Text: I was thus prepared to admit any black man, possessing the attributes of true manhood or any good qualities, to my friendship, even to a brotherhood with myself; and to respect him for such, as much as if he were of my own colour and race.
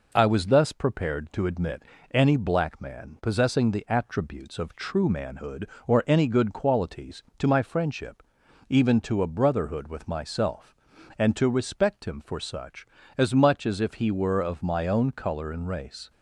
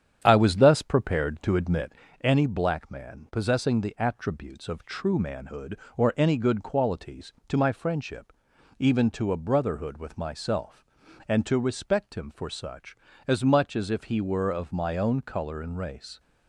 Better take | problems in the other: first | starts louder than the rest; strong; until 1.9 s; 9.5 dB // pauses between "admit" and "any"; slight; at 1.9 s; 0.28 s long; slight in the first

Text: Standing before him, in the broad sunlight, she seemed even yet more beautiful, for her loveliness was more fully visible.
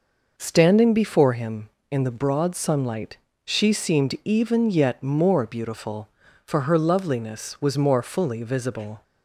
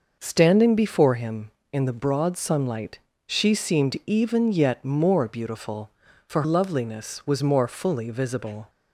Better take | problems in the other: first | skips "her"; at 6.4 s

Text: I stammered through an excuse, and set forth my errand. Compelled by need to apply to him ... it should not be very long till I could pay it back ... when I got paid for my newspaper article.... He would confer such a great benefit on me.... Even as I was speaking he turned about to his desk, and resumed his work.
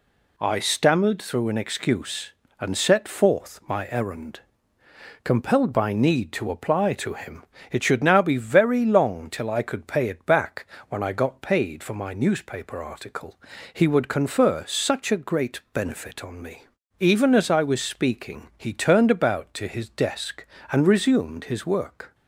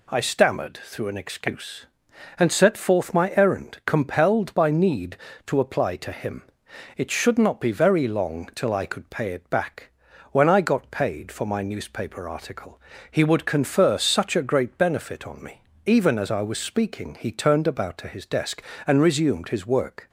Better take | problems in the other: second | says "now" for "not"; at 8.0 s

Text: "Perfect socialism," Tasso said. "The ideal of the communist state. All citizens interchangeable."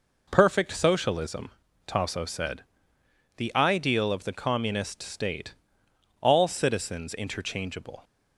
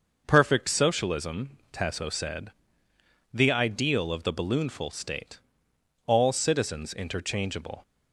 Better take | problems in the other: first | starts louder than the rest; noticeable; until 1.2 s; 6 dB // says "balloonful" for "communist"; at 4.3 s

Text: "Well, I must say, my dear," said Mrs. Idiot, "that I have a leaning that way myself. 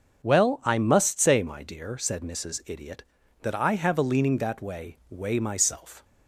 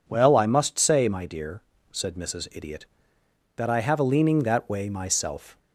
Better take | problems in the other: second | starts louder than the rest; until 1.2 s; 6.5 dB // says "way" twice; at 5.0 s

